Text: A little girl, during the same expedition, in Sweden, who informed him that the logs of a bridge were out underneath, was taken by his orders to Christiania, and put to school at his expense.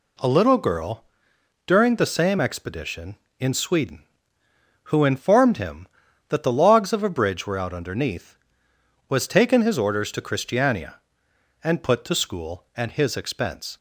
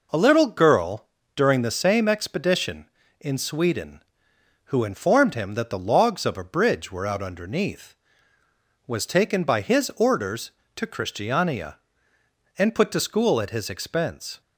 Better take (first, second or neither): second